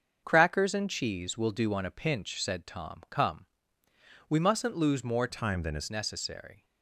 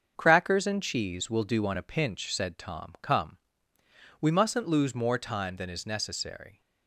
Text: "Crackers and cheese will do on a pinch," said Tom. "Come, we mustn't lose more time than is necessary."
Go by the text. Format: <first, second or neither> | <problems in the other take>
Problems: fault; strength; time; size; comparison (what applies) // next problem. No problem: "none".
second | starts louder than the rest; until 1.2 s; 7 dB; also in the second // changes voice from "time" to "is"; from 5.2 to 5.9 s; 0.7 s long